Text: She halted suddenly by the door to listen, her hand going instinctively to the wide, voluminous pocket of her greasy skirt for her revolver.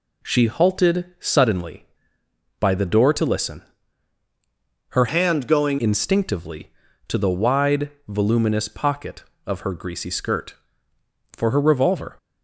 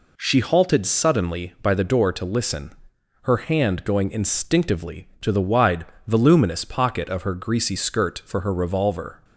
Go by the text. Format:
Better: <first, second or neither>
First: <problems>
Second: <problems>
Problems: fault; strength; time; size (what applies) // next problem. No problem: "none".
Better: second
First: changes voice from "hand" to "going"; from 5.0 to 5.7 s; 0.7 s long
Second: none